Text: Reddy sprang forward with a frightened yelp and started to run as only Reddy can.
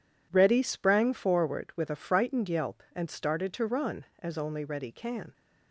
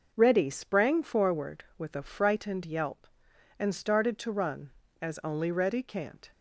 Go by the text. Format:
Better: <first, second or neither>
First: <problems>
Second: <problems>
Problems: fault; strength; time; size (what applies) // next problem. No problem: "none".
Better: first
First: none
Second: says "can't" for "can"; at 5.8 s